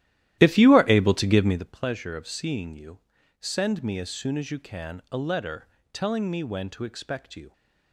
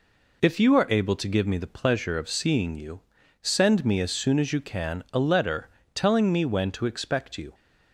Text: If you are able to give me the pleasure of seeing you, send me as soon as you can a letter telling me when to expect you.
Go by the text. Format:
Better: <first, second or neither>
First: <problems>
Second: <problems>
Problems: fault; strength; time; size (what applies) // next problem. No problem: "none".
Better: second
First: starts louder than the rest; strong; until 1.7 s; 13 dB // pauses between "letter" and "telling"; slight; at 5.6 s; 0.26 s long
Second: pauses between "letter" and "telling"; slight; at 5.6 s; 0.26 s long